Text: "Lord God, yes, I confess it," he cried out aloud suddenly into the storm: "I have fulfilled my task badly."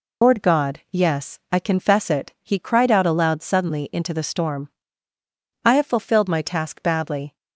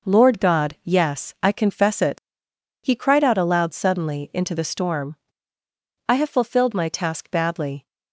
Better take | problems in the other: second | loses the start of "Lord"; at 0.2 s; 115 ms

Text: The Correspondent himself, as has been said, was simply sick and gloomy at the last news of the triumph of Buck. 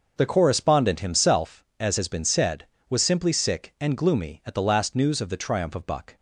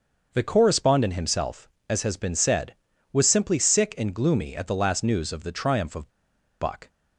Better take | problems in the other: first | starts louder than the rest; until 1.3 s; 6.5 dB; also in the first // pauses between "of" and "Buck"; noticeable; at 6.0 s; 0.50 s long

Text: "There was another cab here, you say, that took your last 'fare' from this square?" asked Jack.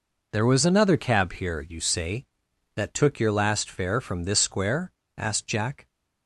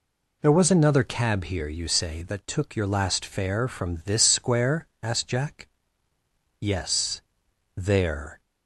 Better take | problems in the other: first | goes on to say "Yes there"; strong; from 6.5 s on; 1.8 s long

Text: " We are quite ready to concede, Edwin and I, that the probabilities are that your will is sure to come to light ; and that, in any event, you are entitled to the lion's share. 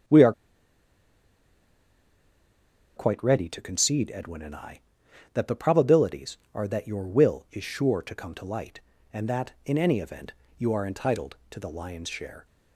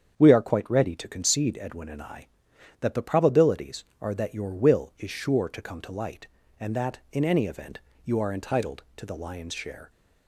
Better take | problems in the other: second | starts louder than the rest; strong; until 3.7 s; 7.5 dB; strong in the second // pauses between "are" and "quite"; strong; at 0.3 s; 2.6 s long

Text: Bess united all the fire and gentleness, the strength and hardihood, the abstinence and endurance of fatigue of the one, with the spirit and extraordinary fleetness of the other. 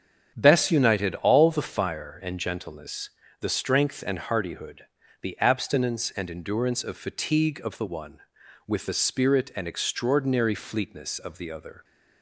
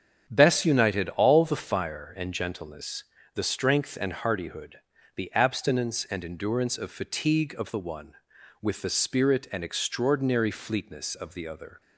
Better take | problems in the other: neither | starts louder than the rest; strong; the same in both

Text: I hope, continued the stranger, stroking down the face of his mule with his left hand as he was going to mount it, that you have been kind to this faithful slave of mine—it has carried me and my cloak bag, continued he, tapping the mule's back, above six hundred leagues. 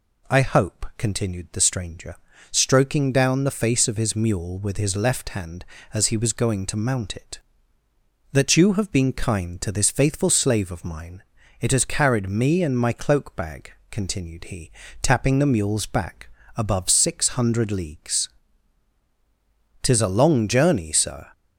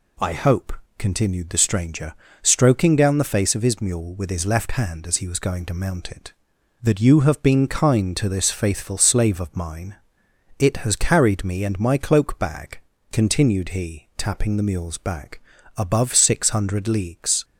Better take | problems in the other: second | goes on to say "Tis a long journey Sir"; from 19.8 s on; 1.4 s long

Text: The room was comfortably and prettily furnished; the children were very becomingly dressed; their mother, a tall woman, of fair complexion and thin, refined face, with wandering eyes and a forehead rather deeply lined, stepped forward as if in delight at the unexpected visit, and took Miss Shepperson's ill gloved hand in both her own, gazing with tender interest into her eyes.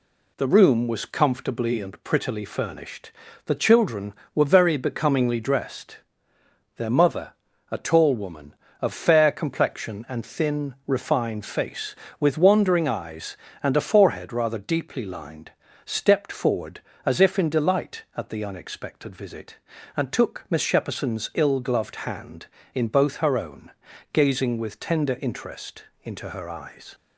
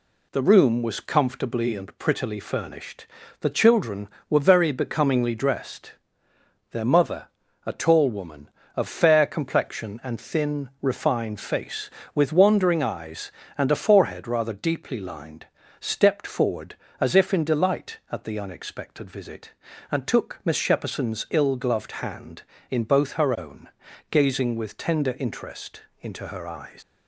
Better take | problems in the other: first | pauses between "interest" and "into"; slight; at 25.8 s; 0.20 s long; slight in the first // leaves "eyes" unfinished; at 26.8 s; 100 ms

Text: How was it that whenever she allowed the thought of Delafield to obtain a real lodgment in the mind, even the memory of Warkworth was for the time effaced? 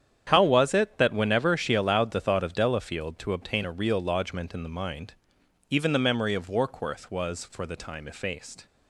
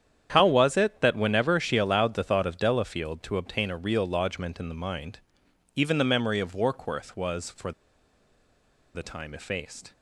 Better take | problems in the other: first | starts louder than the rest; strong; until 1.3 s; 9 dB; strong in the first // pauses between "for" and "the"; at 7.7 s; 1.2 s long

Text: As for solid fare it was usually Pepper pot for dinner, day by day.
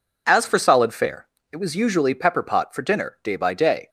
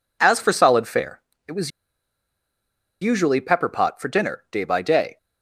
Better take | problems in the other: first | pauses between "fare" and "it"; slight; at 1.2 s; 0.28 s long; slight in the first // pauses between "was" and "usually"; strong; at 1.7 s; 1.3 s long

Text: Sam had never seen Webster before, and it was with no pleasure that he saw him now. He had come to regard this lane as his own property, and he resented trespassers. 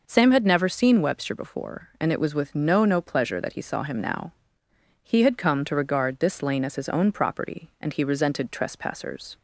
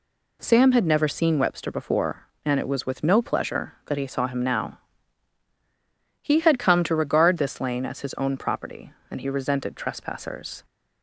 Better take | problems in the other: second | says "no" twice; at 2.8 s

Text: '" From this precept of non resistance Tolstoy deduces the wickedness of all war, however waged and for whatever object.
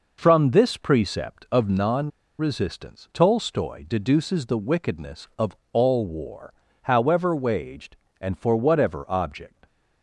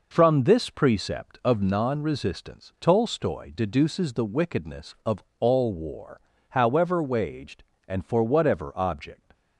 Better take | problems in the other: second | pauses between "non" and "resistance"; slight; at 2.0 s; 0.29 s long // pauses between "of" and "all"; slight; at 5.5 s; 0.16 s long; slight in the second

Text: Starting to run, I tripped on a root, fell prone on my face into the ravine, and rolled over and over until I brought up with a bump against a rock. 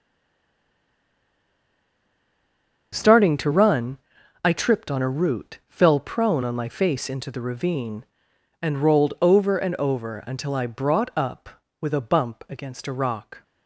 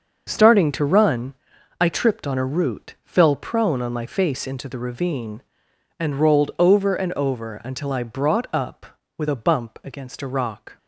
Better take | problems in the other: second | stays silent before the first word; strong; until 2.9 s; 2.9 s long // starts louder than the rest; until 3.9 s; 6.5 dB; also in the second

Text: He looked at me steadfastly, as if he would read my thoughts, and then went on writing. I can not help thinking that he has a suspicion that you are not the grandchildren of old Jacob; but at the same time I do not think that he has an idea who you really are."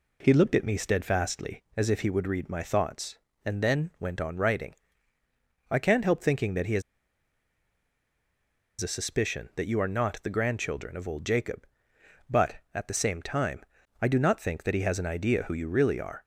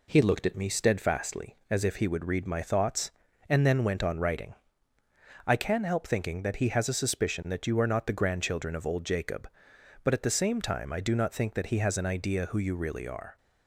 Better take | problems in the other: second | pauses between "has" and "a"; strong; at 6.8 s; 1.9 s long // pauses between "time" and "I"; at 13.6 s; 0.38 s long

